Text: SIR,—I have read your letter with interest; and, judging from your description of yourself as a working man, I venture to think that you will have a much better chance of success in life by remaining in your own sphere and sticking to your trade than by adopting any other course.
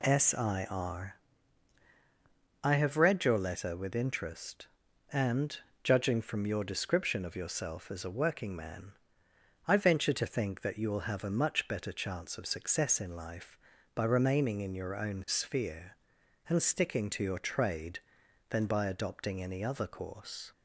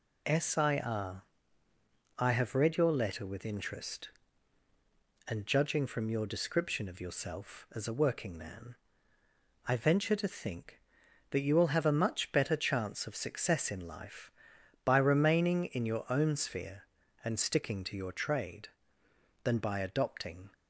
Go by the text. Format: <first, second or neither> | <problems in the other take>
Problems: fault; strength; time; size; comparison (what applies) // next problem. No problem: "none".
first | stops before "any other course"; at 20.5 s